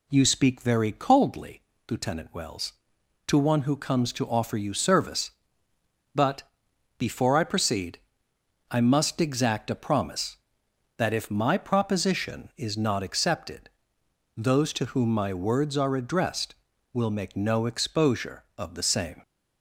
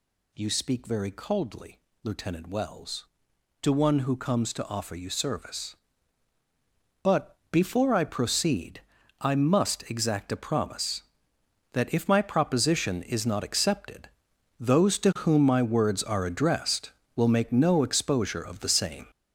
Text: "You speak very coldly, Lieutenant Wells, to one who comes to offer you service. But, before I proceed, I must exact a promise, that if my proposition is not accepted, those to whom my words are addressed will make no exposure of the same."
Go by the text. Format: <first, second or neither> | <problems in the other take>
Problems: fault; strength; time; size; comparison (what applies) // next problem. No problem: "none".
first | gets louder; strong; throughout; 7.5 dB